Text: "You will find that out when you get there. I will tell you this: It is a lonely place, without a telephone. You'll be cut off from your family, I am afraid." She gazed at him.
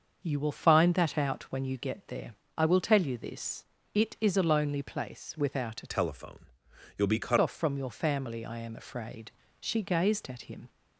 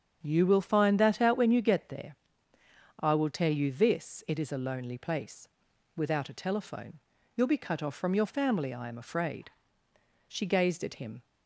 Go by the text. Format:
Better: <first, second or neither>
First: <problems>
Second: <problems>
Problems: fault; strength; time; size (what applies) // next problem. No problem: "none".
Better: second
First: starts louder than the rest; until 1.2 s; 6.5 dB // changes voice from "telephone" to "cut"; from 5.9 to 7.3 s; 1.4 s long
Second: starts louder than the rest; strong; until 1.2 s; 7 dB